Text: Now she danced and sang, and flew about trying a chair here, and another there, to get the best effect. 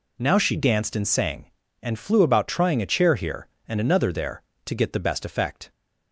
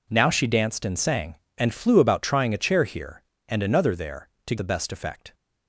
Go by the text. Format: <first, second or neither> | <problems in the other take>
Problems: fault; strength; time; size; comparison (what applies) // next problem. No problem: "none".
first | skips "get"; at 4.5 s